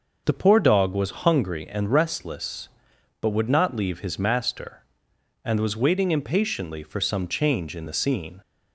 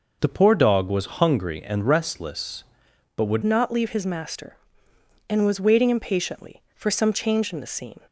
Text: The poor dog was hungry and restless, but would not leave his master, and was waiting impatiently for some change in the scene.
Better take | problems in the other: first | changes voice at "not"; from 3.4 s on; 4.6 s long

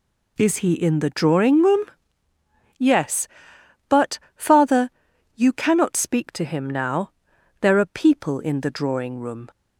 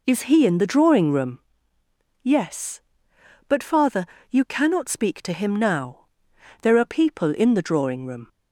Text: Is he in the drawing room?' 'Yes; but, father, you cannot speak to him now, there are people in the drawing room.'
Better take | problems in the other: neither | none

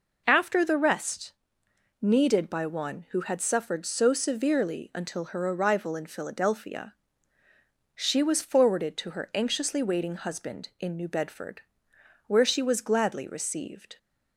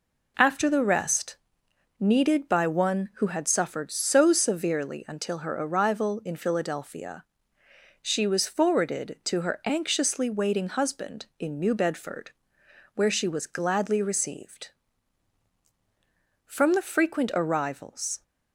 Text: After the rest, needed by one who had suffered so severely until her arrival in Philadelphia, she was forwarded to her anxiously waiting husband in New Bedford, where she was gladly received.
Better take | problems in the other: first | goes on to say "From the frequent arrivals"; strong; from 16.4 s on; 1.7 s long

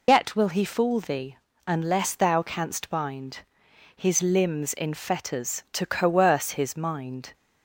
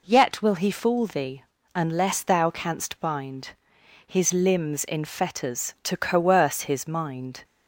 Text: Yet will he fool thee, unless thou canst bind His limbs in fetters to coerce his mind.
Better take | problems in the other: second | loses the start of "Yet"; at 0.0 s; 95 ms // pauses between "bind" and "His"; noticeable; at 3.4 s; 0.50 s long; noticeable in the second

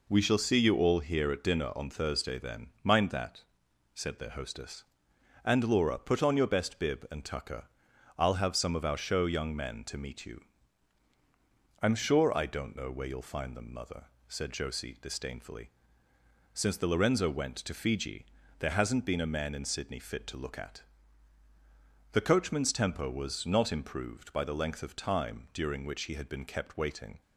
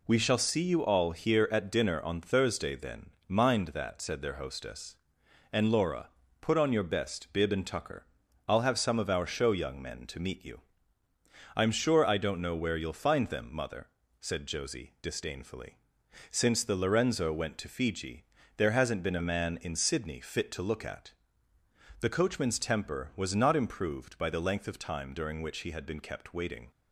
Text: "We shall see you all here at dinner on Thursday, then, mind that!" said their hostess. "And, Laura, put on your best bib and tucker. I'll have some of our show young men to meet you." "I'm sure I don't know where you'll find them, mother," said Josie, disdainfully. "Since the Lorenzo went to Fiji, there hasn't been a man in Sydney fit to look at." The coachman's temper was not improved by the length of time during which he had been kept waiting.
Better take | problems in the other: neither | none

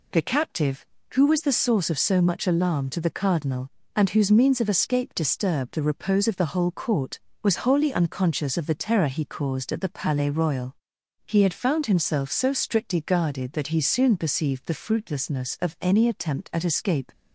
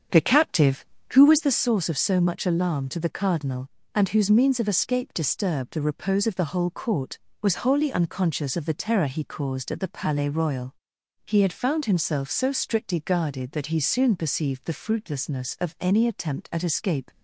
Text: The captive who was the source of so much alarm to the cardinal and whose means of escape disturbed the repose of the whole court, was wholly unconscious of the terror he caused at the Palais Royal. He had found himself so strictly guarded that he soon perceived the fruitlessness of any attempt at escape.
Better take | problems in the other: first | starts louder than the rest; strong; until 1.6 s; 7.5 dB

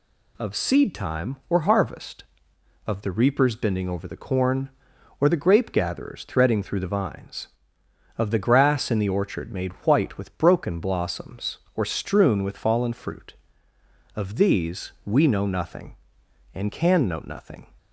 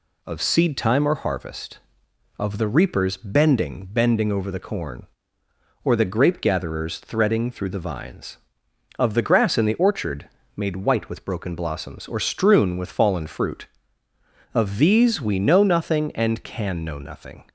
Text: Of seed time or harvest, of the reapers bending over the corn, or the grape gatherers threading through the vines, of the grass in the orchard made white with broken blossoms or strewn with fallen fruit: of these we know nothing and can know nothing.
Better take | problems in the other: first | says "bending" twice; at 3.8 s // pauses between "orchard" and "made"; slight; at 10.2 s; 0.28 s long

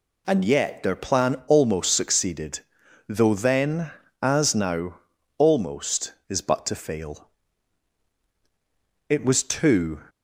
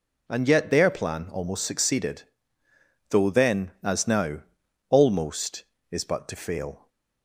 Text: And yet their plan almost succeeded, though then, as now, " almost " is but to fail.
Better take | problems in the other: second | goes on to say "It was two"; noticeable; from 9.0 s on; 0.92 s long

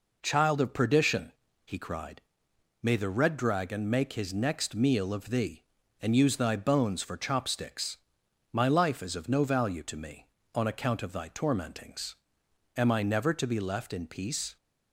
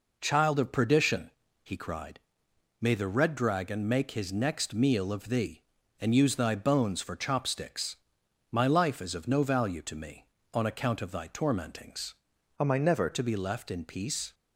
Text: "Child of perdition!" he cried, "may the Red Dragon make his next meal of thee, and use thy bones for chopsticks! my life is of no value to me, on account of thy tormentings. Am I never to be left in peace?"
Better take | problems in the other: first | changes voice from "Am" to "never"; from 12.5 to 13.1 s; 0.6 s long

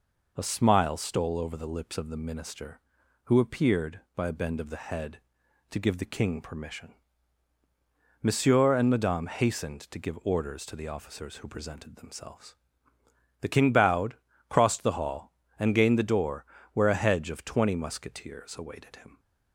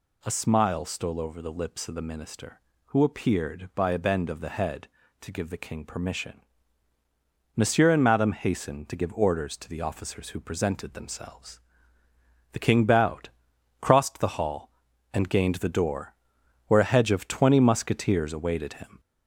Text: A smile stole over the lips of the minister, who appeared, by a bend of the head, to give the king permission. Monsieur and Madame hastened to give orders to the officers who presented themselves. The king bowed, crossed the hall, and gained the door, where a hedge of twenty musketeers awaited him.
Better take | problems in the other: first | gets louder; slight; throughout; 3 dB

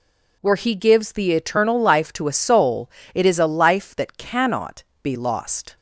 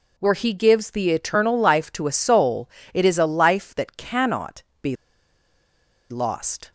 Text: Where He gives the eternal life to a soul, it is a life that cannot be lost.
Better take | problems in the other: first | pauses between "cannot" and "be"; slight; at 4.6 s; 0.18 s long; slight in the first // pauses between "be" and "lost"; at 4.9 s; 1.1 s long

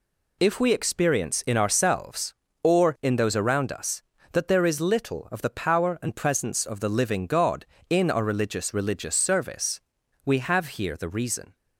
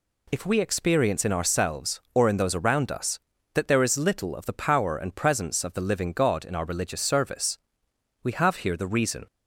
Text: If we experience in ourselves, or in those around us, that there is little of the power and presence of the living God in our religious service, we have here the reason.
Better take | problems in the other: second | says "religious" twice; at 8.7 s

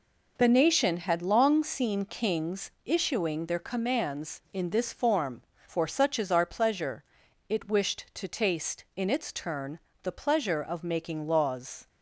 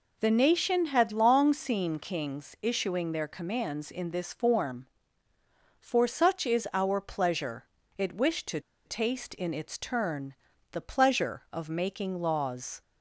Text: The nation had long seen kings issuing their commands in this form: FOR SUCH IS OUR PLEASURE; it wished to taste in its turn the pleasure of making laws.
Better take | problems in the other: first | pauses between "to" and "taste"; slight; at 8.5 s; 0.26 s long // pauses between "turn" and "the"; at 10.3 s; 0.38 s long; slight in the first

